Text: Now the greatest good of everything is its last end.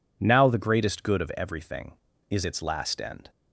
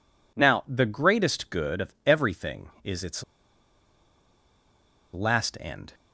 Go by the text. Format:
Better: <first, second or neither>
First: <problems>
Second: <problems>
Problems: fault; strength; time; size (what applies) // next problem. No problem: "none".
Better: first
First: none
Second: pauses between "its" and "last"; strong; at 3.2 s; 1.9 s long